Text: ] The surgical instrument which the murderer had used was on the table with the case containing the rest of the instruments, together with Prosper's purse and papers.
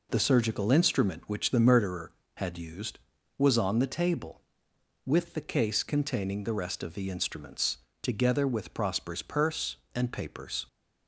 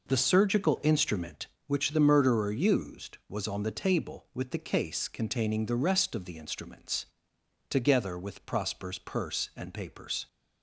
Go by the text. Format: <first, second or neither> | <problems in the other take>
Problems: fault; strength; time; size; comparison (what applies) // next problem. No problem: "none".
first | skips "had"; at 2.4 s